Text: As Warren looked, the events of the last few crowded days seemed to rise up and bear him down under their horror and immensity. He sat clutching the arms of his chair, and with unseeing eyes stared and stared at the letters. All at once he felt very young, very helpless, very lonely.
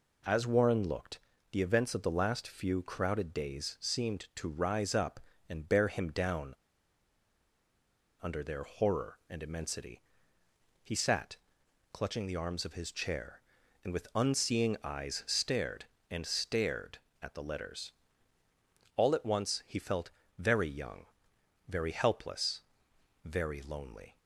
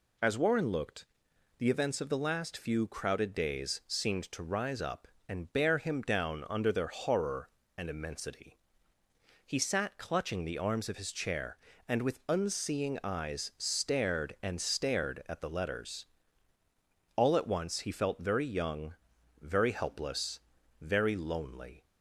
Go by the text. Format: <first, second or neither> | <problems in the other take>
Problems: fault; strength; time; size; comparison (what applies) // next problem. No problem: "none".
second | pauses between "down" and "under"; strong; at 6.5 s; 1.6 s long // pauses between "sat" and "clutching"; noticeable; at 11.3 s; 0.56 s long // pauses between "felt" and "very"; slight; at 20.1 s; 0.26 s long